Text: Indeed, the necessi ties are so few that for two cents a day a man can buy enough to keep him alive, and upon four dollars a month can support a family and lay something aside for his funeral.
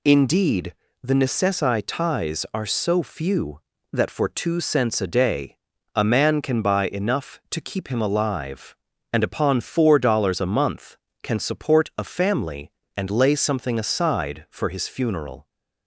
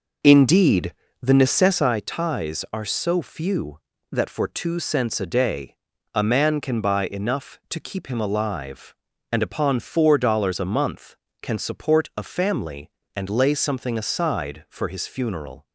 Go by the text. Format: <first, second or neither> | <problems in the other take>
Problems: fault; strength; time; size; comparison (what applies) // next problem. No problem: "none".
first | starts louder than the rest; noticeable; until 1.9 s; 5.5 dB // pauses between "day" and "a"; at 5.7 s; 0.38 s long; also in the first